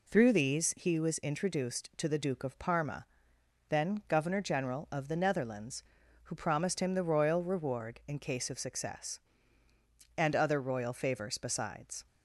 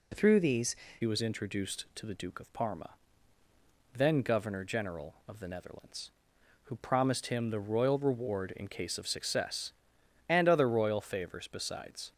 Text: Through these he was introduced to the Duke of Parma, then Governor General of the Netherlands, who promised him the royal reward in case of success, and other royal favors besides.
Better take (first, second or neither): first